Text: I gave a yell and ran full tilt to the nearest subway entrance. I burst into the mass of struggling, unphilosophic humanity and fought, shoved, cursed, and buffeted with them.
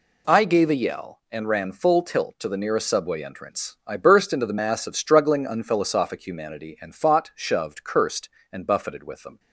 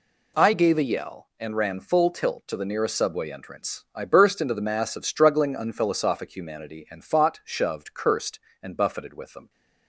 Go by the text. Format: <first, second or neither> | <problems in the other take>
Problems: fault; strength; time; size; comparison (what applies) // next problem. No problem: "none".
neither | none